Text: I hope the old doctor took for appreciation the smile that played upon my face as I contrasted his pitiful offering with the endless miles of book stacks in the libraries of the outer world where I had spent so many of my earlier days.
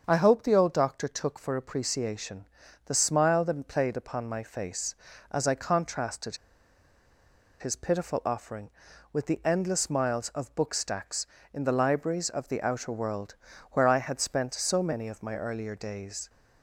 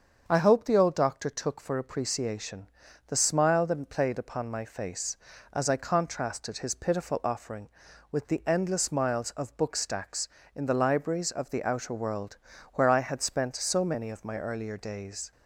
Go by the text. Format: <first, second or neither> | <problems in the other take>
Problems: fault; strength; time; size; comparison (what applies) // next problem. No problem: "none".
second | starts louder than the rest; until 1.0 s; 7 dB; also in the second // pauses between "appreciation" and "the"; at 2.4 s; 0.38 s long; also in the second // pauses between "contrasted" and "his"; at 6.3 s; 1.2 s long // pauses between "world" and "where"; at 13.3 s; 0.38 s long; also in the second